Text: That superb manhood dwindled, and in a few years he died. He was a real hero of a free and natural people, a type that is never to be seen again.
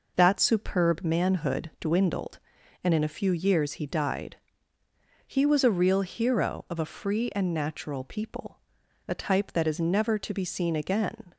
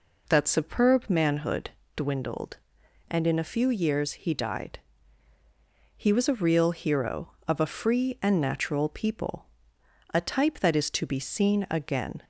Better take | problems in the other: first | pauses between "manhood" and "dwindled"; slight; at 1.6 s; 0.26 s long // skips "never"; at 10.9 s

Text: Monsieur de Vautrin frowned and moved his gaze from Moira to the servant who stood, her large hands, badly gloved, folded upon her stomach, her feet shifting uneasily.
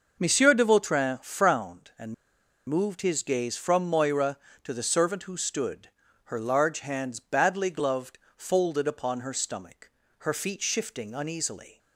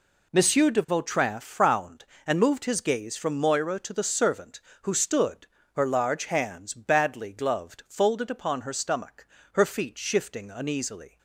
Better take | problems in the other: second | pauses between "and" and "moved"; noticeable; at 2.1 s; 0.53 s long

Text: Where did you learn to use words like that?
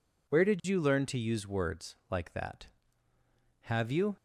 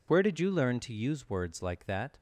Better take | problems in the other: second | goes on to say "Have you"; from 3.6 s on; 0.52 s long

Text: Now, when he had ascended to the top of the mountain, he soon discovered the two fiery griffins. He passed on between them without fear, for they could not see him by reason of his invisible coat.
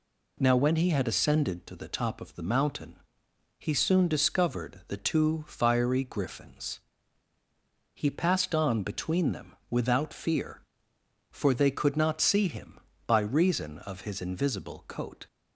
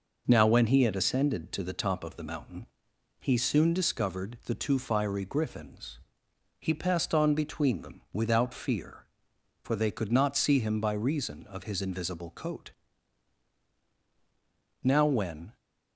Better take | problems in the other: first | goes on to say "Now when"; noticeable; from 14.8 s on; 0.74 s long

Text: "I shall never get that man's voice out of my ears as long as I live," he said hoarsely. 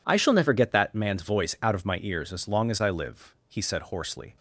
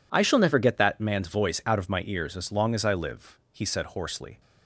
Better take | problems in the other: neither | none

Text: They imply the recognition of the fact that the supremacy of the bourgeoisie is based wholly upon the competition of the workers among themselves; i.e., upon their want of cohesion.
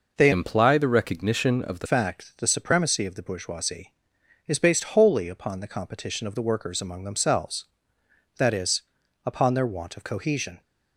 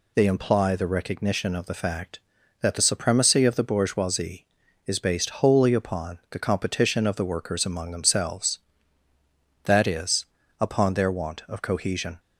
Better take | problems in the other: second | changes voice from "imply" to "the"; from 0.3 to 1.8 s; 1.5 s long

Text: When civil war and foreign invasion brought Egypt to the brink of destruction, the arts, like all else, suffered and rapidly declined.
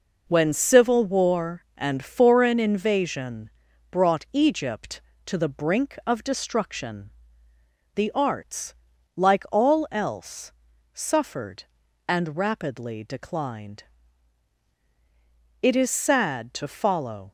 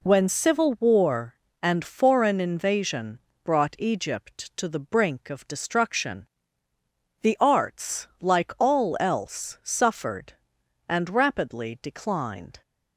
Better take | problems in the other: second | pauses between "invasion" and "brought"; at 3.4 s; 0.42 s long; slight in the second // goes on to say "It is sad to follow"; strong; from 15.6 s on; 1.7 s long

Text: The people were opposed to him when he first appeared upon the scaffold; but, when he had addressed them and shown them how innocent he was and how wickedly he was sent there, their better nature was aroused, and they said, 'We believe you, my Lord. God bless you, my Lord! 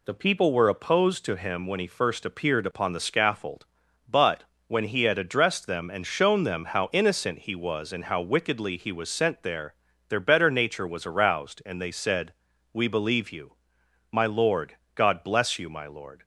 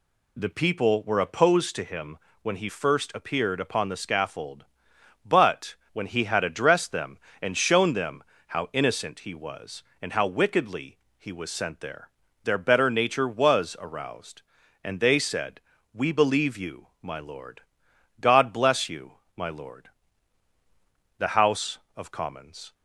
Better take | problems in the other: first | pauses between "him" and "when"; slight; at 2.1 s; 0.28 s long // pauses between "them" and "how"; slight; at 8.2 s; 0.26 s long // pauses between "wickedly" and "he"; slight; at 10.9 s; 0.20 s long // goes on to say "The House of Commons"; from 21.1 s on; 1.5 s long

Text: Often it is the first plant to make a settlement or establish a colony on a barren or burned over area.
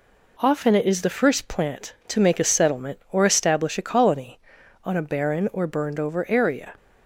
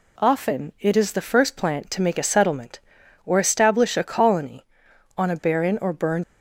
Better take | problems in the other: first | stops before "over area"; at 6.2 s

